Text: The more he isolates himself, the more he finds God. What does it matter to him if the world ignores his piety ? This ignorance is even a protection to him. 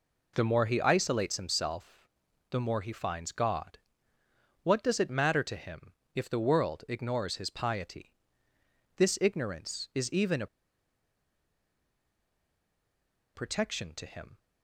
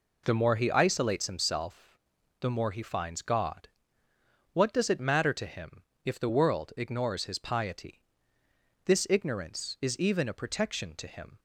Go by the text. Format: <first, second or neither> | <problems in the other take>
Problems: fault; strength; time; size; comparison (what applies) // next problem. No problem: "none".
second | pauses between "him" and "if"; slight; at 5.9 s; 0.20 s long; slight in the second // pauses between "a" and "protection"; strong; at 10.4 s; 2.8 s long